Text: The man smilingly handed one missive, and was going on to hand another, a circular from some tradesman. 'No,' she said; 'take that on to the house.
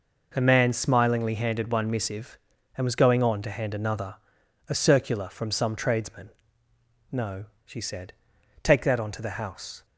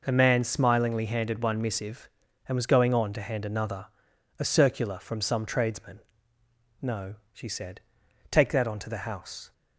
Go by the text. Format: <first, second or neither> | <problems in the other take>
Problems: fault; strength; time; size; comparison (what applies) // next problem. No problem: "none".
neither | none